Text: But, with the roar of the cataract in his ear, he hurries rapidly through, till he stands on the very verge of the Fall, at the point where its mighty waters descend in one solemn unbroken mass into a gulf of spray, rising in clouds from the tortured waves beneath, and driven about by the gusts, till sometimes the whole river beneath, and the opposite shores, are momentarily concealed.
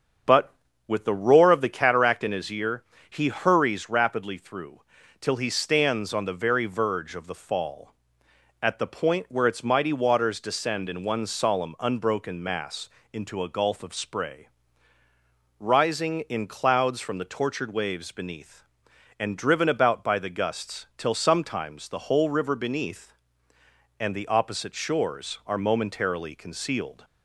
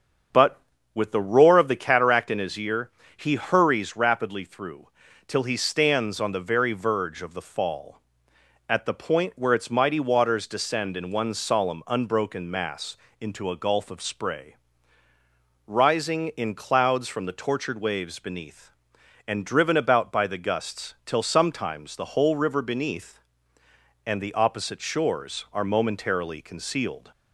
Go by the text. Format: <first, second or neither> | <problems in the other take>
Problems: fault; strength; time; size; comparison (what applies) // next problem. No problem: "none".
neither | starts louder than the rest; strong; the same in both // pauses between "mass" and "into"; slight; the same in both